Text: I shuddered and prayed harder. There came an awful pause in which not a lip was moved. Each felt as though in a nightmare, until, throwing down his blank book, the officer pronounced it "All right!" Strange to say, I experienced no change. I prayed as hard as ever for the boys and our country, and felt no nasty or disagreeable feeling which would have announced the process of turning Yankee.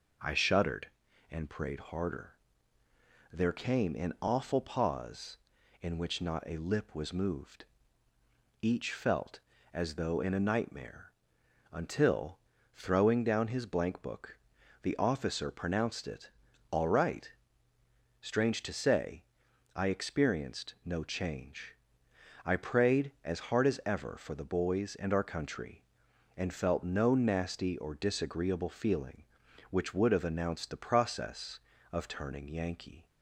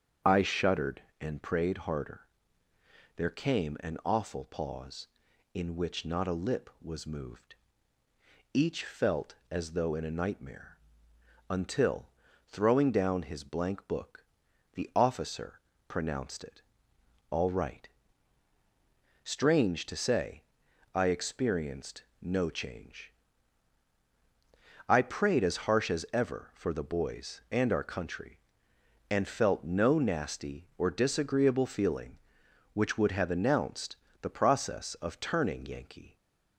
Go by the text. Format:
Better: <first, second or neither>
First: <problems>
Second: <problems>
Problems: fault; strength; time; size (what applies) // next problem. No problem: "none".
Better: first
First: pauses between "it" and "All"; at 16.3 s; 0.38 s long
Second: starts louder than the rest; strong; until 1.4 s; 7 dB // pauses between "officer" and "pronounced"; slight; at 15.5 s; 0.30 s long // pauses between "it" and "All"; noticeable; at 16.6 s; 0.68 s long // pauses between "experienced" and "no"; slight; at 22.0 s; 0.18 s long // says "harsh" for "hard"; at 25.6 s // pauses between "announced" and "the"; slight; at 33.9 s; 0.28 s long